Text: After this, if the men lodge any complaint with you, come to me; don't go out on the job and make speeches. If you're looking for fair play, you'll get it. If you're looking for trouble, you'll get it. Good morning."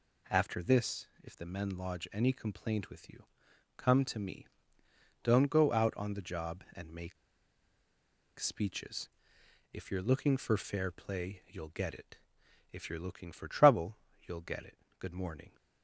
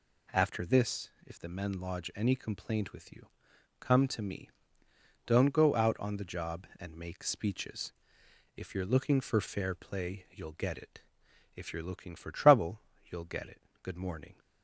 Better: second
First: pauses between "make" and "speeches"; at 7.1 s; 1.2 s long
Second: none

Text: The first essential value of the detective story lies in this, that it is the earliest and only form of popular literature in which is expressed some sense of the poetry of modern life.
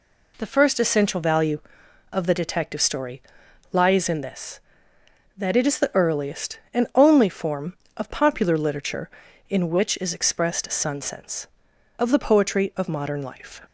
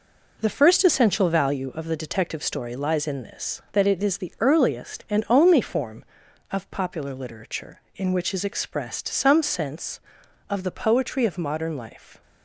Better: second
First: pauses between "story" and "lies"; noticeable; at 3.2 s; 0.50 s long // says "sun" for "some"; at 10.7 s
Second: none

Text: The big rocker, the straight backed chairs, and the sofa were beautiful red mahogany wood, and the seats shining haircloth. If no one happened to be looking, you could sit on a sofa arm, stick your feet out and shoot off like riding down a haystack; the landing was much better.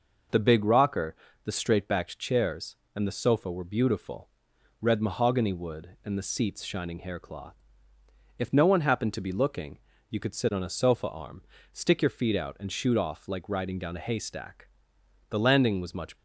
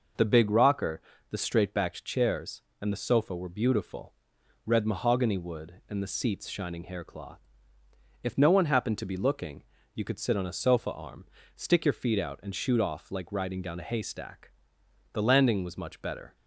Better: second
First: pauses between "beautiful" and "red"; noticeable; at 4.2 s; 0.54 s long // stops before "better"; at 16.1 s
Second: pauses between "beautiful" and "red"; noticeable; at 4.1 s; 0.54 s long

